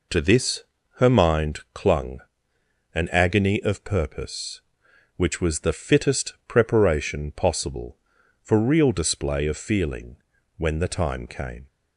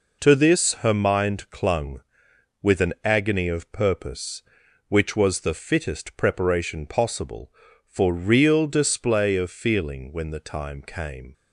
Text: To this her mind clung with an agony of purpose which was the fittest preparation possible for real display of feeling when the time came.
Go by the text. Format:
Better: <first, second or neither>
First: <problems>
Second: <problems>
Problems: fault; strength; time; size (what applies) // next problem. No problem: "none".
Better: second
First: pauses between "this" and "her"; slight; at 0.6 s; 0.34 s long // skips "with"; at 2.5 s // pauses between "feeling" and "when"; at 10.1 s; 0.40 s long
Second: none